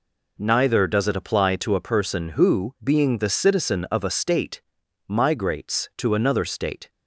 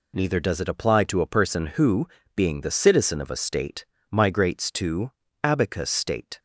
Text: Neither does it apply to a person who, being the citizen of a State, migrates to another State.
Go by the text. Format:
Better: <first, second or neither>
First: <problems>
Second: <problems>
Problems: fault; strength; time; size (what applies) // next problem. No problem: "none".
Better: first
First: none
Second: says "abacus" for "another"; at 5.4 s